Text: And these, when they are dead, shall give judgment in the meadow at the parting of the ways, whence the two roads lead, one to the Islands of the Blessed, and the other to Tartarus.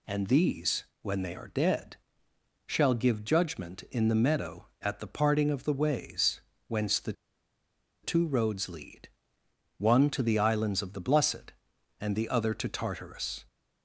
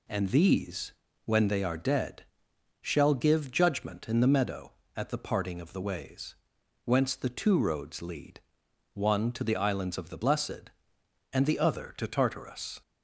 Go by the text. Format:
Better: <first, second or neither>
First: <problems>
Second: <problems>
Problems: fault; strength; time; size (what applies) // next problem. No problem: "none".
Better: second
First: pauses between "the" and "two"; noticeable; at 7.1 s; 0.90 s long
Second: none